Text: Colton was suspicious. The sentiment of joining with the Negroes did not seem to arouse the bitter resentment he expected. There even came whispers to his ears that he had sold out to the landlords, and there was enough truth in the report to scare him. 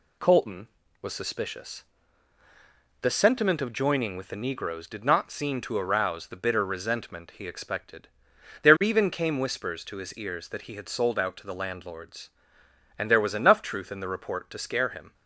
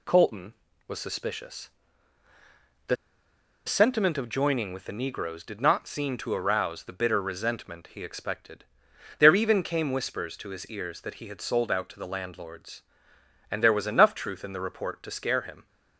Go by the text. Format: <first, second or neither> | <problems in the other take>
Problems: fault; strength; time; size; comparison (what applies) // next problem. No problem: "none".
first | pauses between "The" and "sentiment"; noticeable; at 2.9 s; 0.70 s long